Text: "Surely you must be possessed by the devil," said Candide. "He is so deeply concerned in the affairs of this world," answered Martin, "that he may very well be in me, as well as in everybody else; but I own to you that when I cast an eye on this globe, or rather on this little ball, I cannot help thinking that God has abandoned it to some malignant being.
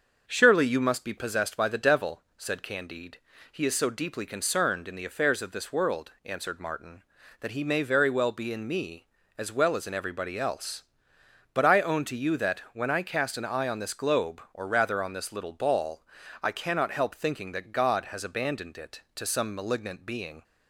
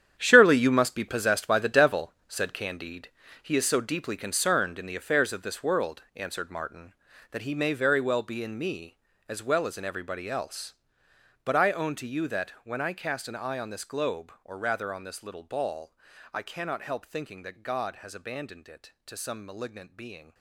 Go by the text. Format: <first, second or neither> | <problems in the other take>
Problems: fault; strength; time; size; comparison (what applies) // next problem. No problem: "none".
first | gets quieter; strong; throughout; 12.5 dB // starts louder than the rest; strong; until 1.1 s; 9.5 dB; also in the first